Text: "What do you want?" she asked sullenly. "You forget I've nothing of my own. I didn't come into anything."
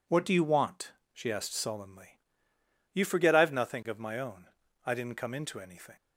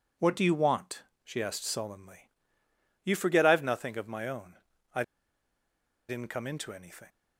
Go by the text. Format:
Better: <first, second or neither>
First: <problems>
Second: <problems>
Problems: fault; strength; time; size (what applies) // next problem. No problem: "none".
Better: first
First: none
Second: pauses between "I" and "didn't"; at 5.0 s; 1.0 s long